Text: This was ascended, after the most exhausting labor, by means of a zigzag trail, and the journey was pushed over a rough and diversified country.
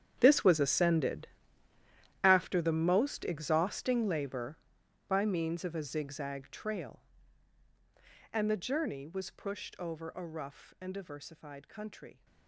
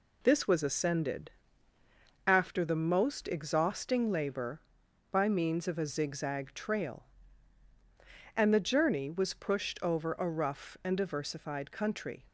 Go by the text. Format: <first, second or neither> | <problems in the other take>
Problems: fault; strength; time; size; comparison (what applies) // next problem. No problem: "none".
second | gets quieter; strong; throughout; 16.5 dB